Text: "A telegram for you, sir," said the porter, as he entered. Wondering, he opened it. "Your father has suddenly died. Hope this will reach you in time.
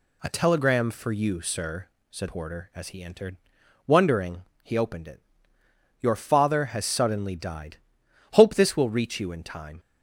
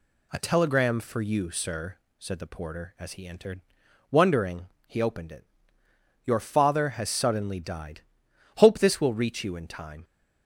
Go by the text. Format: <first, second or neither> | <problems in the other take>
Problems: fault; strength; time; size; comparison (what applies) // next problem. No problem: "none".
second | skips "the"; at 2.2 s